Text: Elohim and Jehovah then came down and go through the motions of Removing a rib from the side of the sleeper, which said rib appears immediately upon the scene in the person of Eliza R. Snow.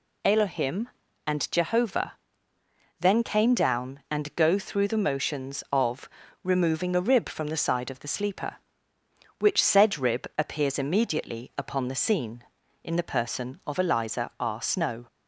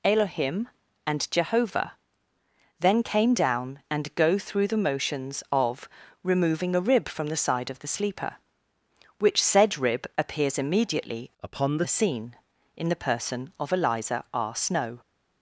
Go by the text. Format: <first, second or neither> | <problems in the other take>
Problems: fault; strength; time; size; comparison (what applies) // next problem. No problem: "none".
first | pauses between "Jehovah" and "then"; noticeable; at 1.9 s; 0.86 s long; noticeable in the first // pauses between "of" and "Removing"; slight; at 5.9 s; 0.32 s long; slight in the first // changes voice from "upon" to "the"; from 11.4 to 11.8 s; 0.4 s long